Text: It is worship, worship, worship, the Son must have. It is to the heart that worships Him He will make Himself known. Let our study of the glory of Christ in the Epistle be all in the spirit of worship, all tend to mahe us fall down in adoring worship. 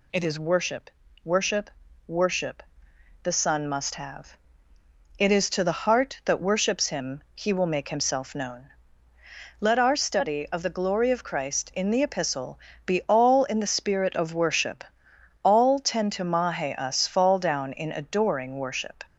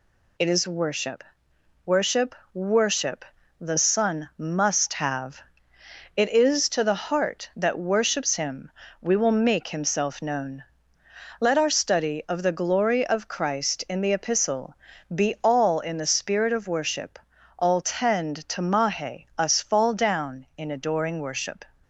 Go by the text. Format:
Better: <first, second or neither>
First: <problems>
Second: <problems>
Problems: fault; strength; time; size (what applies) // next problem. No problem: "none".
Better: first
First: pauses between "Epistle" and "be"; slight; at 12.5 s; 0.26 s long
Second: says "We" for "He"; at 9.0 s // pauses between "Epistle" and "be"; slight; at 14.7 s; 0.36 s long